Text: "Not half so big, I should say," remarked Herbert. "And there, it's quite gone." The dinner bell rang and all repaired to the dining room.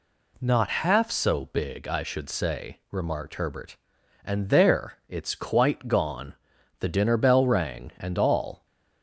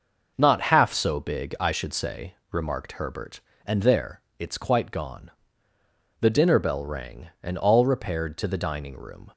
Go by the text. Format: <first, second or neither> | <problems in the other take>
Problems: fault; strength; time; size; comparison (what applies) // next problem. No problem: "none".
second | stops before "repaired to the dining room"; at 8.6 s